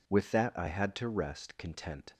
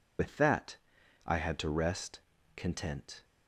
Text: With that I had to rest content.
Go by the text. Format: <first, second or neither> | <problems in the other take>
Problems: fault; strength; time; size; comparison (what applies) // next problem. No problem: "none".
first | loses the start of "With"; at 0.1 s; 105 ms // pauses between "that" and "I"; noticeable; at 0.7 s; 0.50 s long // pauses between "rest" and "content"; slight; at 2.1 s; 0.36 s long